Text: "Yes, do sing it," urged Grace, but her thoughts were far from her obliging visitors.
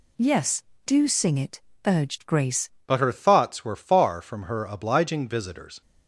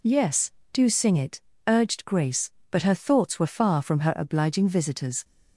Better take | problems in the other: second | changes voice at "but"; from 2.8 s on; 3.0 s long

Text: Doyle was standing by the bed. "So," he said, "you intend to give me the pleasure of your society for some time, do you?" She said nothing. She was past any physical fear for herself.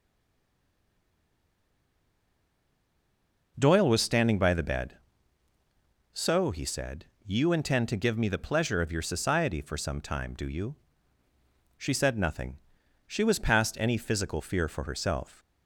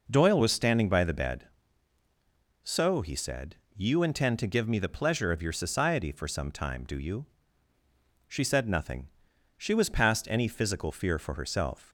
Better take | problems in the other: second | stays silent before the first word; strong; until 3.5 s; 3.5 s long

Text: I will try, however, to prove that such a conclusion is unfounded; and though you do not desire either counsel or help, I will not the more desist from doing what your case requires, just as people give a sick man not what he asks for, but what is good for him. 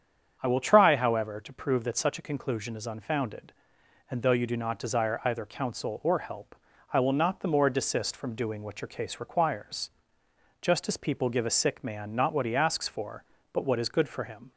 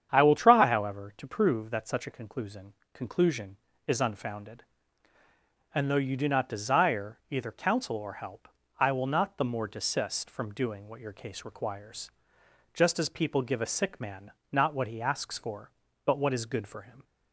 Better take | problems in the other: first | starts louder than the rest; strong; until 1.1 s; 8.5 dB; strong in the first // says "conclusion" twice; at 2.9 s // pauses between "man" and "not"; slight; at 14.3 s; 0.20 s long

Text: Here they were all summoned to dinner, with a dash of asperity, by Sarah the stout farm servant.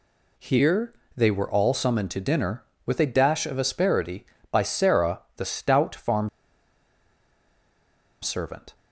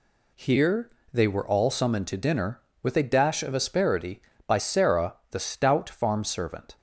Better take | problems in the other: second | pauses between "Here" and "they"; slight; at 0.9 s; 0.24 s long; slight in the second // pauses between "Sarah" and "the"; slight; at 5.2 s; 0.16 s long; slight in the second // pauses between "farm" and "servant"; strong; at 6.2 s; 1.9 s long

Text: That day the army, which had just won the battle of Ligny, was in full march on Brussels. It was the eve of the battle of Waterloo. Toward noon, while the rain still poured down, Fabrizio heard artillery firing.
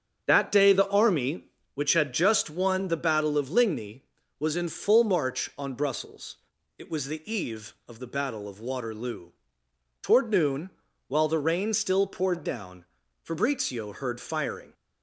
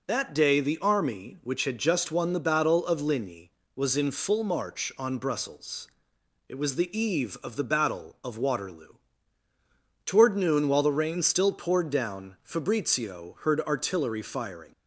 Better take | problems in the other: second | starts louder than the rest; until 1.2 s; 7 dB // skips "artillery"; at 14.1 s

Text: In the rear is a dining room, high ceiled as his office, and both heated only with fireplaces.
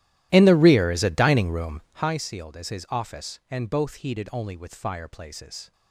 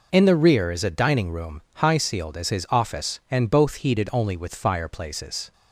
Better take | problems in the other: second | starts louder than the rest; strong; until 2.1 s; 14 dB

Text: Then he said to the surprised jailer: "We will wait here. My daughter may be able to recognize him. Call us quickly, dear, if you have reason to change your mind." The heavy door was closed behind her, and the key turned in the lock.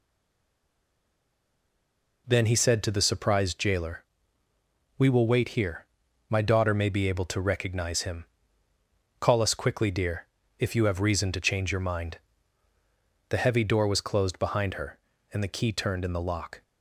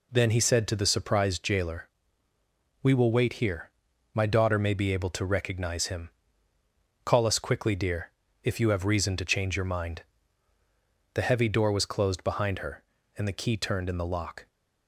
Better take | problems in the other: second | stays silent before the first word; until 2.2 s; 2.2 s long

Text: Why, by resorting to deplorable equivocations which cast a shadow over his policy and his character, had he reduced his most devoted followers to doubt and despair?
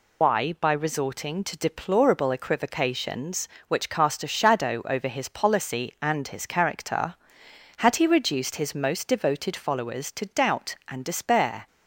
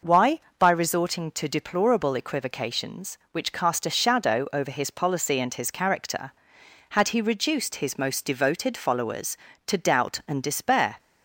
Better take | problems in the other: second | loses the start of "Why"; at 0.2 s; 105 ms

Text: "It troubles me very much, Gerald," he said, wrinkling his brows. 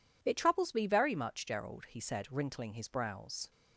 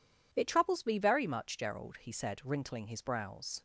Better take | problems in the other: neither | none

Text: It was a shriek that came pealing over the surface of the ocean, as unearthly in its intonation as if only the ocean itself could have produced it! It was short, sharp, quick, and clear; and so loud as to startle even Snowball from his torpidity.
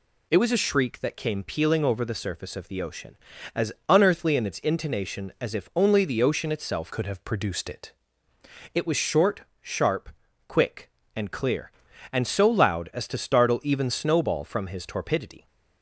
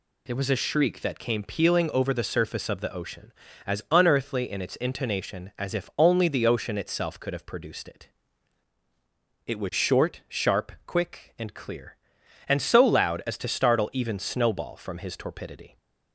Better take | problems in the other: second | pauses between "as" and "unearthly"; slight; at 3.7 s; 0.16 s long // changes voice from "could" to "it"; from 6.9 to 7.9 s; 1.0 s long

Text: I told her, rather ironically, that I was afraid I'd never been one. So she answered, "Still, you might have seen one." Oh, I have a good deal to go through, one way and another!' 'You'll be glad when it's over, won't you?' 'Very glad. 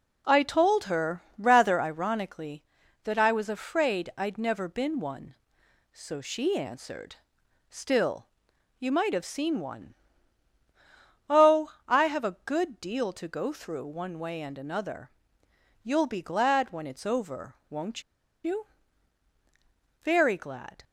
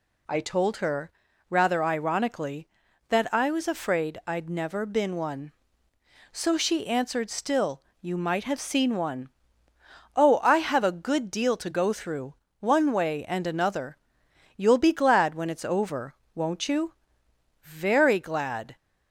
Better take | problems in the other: second | pauses between "won't" and "you"; at 18.0 s; 0.42 s long

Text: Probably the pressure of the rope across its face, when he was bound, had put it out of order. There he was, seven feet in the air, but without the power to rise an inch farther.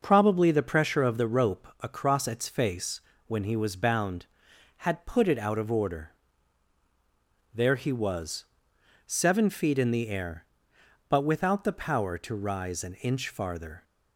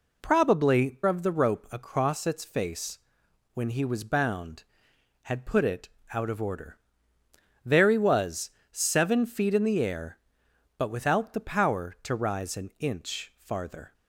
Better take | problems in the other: first | skips "the pressure"; at 1.0 s // pauses between "it" and "out"; slight; at 5.8 s; 0.24 s long

